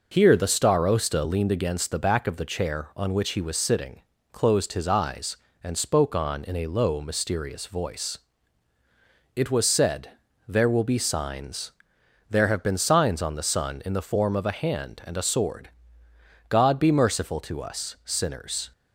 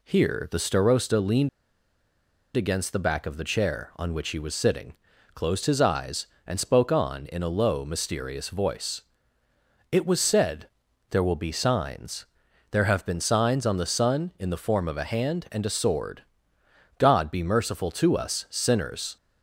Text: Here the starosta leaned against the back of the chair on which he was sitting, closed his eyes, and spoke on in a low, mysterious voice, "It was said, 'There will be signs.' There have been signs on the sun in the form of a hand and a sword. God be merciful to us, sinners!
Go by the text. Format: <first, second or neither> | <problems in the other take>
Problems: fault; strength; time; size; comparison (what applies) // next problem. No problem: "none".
first | pauses between "leaned" and "against"; at 1.4 s; 1.0 s long